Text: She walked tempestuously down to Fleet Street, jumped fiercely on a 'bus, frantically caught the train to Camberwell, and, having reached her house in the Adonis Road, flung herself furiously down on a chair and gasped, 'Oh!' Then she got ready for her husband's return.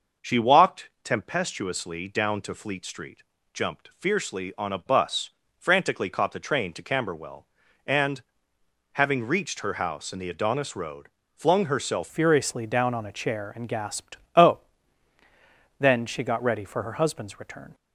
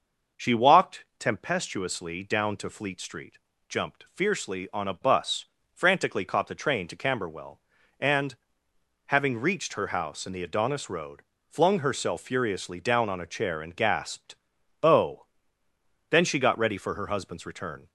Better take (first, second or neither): second